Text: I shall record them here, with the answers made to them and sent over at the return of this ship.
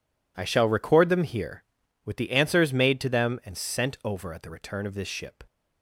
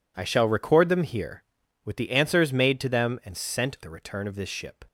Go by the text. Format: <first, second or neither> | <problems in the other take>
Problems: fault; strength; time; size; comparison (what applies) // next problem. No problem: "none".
first | skips "over at"; at 3.8 s